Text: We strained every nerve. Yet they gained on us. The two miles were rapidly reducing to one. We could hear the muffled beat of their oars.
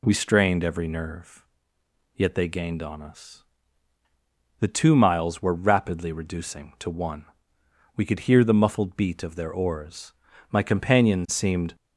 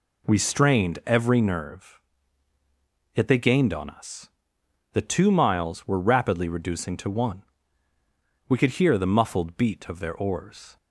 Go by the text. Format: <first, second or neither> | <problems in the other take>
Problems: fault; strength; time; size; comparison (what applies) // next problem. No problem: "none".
second | goes on to say "My companion seemed"; noticeable; from 10.5 s on; 1.2 s long